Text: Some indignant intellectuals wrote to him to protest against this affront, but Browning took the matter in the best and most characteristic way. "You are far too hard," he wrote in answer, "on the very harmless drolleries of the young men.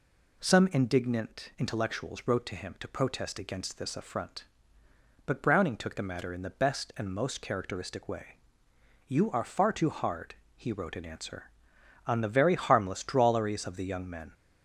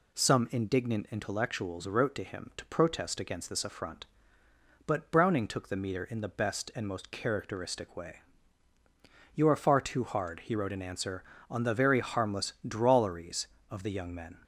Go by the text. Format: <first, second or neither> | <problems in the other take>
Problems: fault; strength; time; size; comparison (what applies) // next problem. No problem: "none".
first | says "meter" for "matter"; at 5.7 s